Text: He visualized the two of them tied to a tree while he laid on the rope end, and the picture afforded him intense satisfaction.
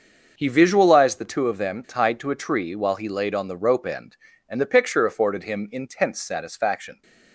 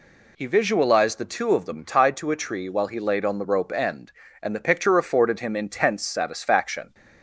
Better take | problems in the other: second | gets quieter; strong; throughout; 11.5 dB

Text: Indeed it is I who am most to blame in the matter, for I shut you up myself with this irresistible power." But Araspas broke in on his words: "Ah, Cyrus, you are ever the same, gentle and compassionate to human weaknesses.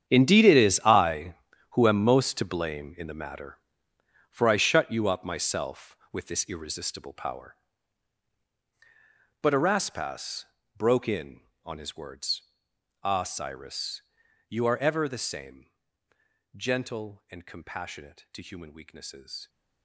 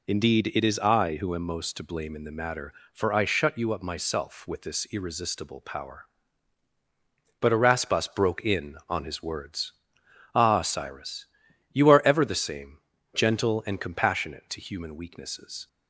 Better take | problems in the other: second | gets quieter; strong; throughout; 15 dB // pauses between "Araspas" and "broke"; slight; at 10.4 s; 0.32 s long

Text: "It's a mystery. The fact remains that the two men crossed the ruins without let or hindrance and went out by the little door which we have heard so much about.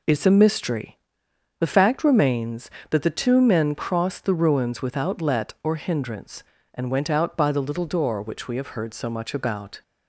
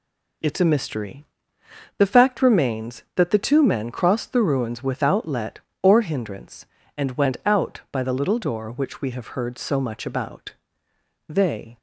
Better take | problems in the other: first | goes on to say "They"; from 11.2 s on; 0.50 s long

